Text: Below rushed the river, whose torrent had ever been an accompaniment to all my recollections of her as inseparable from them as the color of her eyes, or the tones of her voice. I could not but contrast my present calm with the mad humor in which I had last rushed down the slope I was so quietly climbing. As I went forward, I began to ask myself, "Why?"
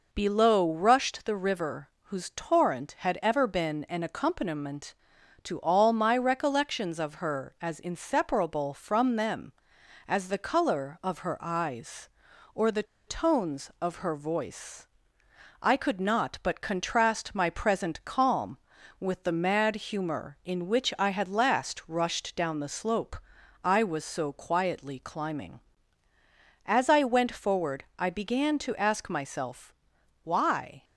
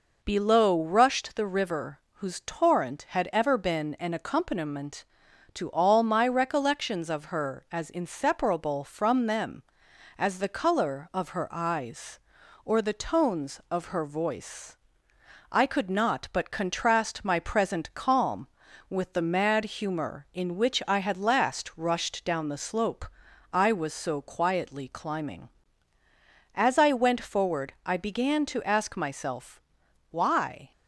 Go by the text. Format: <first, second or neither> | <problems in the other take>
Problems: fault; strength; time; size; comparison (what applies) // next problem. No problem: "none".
second | pauses between "the" and "tones"; slight; at 12.8 s; 0.23 s long // pauses between "slope" and "I"; at 23.1 s; 0.44 s long; also in the second